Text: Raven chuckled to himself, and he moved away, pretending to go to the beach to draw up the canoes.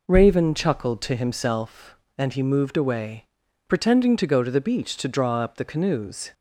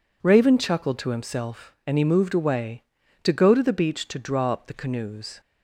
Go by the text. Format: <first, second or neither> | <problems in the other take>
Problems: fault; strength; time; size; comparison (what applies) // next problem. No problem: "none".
first | skips "pretending"; at 3.0 s